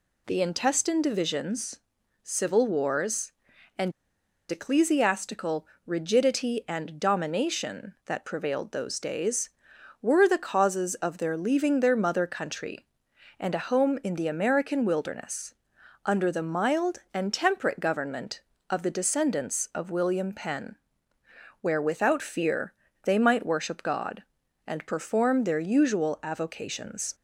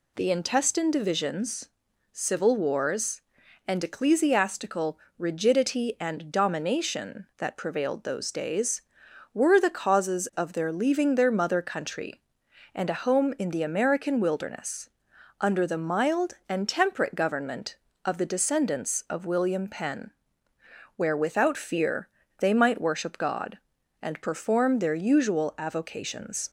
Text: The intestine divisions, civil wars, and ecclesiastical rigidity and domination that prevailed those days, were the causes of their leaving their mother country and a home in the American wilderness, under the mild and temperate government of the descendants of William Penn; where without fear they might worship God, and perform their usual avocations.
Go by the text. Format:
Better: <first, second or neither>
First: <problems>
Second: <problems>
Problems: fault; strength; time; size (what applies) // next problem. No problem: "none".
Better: second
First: pauses between "and" and "ecclesiastical"; noticeable; at 3.9 s; 0.58 s long // pauses between "ecclesiastical" and "rigidity"; slight; at 5.6 s; 0.22 s long // pauses between "fear" and "they"; slight; at 22.7 s; 0.32 s long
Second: pauses between "ecclesiastical" and "rigidity"; slight; at 4.9 s; 0.22 s long // pauses between "fear" and "they"; slight; at 22.0 s; 0.32 s long